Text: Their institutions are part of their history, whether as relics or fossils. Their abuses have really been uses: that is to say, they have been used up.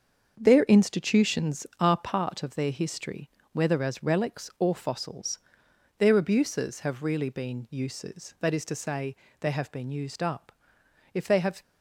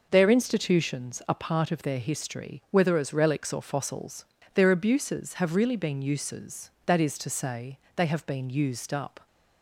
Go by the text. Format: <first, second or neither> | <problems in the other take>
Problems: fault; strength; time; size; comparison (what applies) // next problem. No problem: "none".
second | starts louder than the rest; until 1.3 s; 6.5 dB // goes on to say "If they have"; slight; from 11.1 s on; 0.48 s long